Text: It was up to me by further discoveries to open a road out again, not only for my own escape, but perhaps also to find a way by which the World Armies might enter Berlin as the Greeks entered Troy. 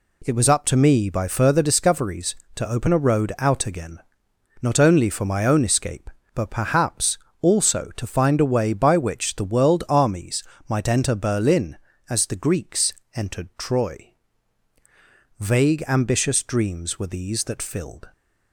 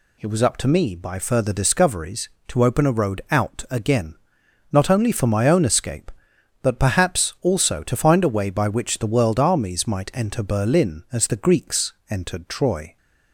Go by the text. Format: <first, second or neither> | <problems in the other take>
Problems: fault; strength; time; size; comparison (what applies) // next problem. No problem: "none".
second | pauses between "perhaps" and "also"; slight; at 7.1 s; 0.22 s long // pauses between "Armies" and "might"; slight; at 10.4 s; 0.24 s long // pauses between "Greeks" and "entered"; slight; at 12.9 s; 0.22 s long; slight in the second // goes on to say "Vague ambitious dreams were these that filled"; strong; from 15.3 s on; 2.7 s long